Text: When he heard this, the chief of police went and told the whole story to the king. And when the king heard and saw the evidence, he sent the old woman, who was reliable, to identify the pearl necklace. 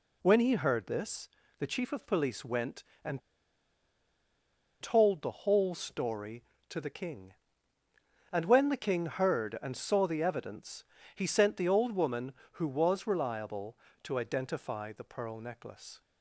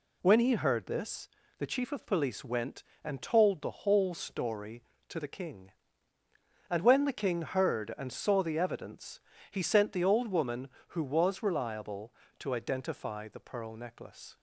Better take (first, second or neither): second